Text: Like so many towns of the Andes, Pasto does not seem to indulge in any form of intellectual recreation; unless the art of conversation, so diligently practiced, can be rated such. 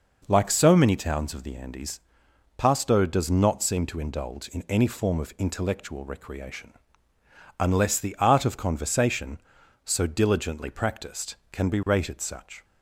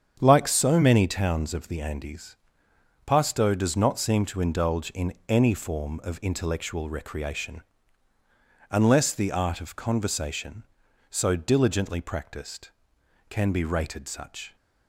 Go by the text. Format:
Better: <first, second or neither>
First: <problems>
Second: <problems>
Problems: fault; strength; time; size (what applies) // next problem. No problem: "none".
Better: first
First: none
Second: starts louder than the rest; strong; until 1.2 s; 8 dB // pauses between "in" and "any"; slight; at 5.1 s; 0.16 s long